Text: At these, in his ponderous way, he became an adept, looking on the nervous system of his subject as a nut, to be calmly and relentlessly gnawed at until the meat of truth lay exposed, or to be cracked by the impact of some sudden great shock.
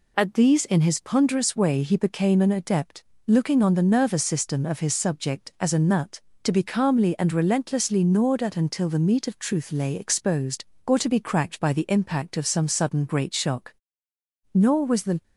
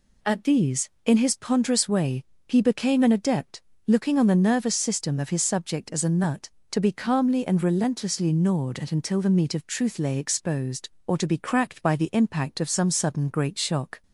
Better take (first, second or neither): second